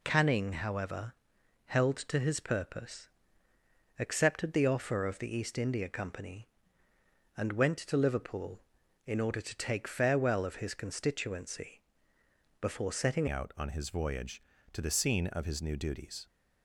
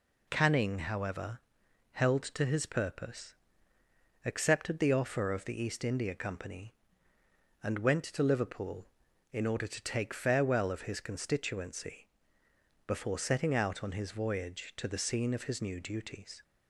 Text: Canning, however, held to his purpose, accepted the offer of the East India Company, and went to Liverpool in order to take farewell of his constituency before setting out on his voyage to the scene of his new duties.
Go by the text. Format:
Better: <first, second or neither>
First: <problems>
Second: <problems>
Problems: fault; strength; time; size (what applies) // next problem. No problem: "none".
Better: second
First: pauses between "constituency" and "before"; noticeable; at 11.8 s; 0.80 s long // changes voice at "out"; from 13.2 s on; 3.0 s long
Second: pauses between "constituency" and "before"; noticeable; at 12.0 s; 0.80 s long